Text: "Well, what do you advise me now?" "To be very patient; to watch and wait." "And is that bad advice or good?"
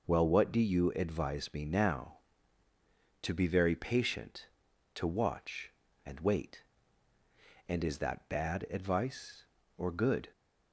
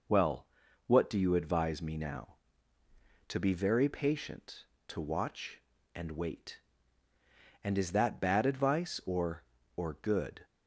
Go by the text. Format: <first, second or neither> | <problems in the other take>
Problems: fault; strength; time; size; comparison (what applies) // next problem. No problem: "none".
first | says "or" twice; at 9.7 s